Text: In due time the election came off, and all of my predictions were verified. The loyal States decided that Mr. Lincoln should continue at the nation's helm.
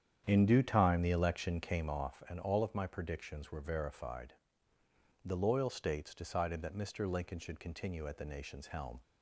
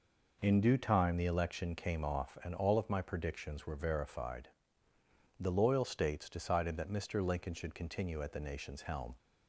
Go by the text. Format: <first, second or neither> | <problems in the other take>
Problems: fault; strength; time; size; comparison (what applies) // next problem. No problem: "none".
second | starts louder than the rest; strong; until 2.0 s; 9 dB